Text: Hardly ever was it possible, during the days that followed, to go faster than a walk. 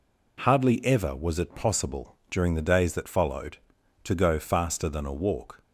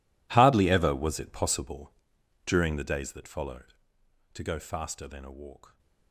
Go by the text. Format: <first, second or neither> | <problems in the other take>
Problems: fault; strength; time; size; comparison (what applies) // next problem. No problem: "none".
first | gets quieter; strong; throughout; 20 dB